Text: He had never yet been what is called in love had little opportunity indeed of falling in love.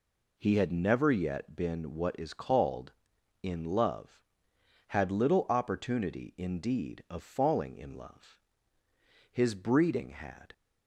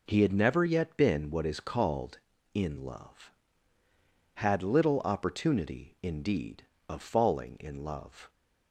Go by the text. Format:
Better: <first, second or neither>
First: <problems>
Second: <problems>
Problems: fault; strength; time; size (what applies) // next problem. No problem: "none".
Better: second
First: goes on to say "His breeding had"; noticeable; from 9.3 s on; 1.2 s long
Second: none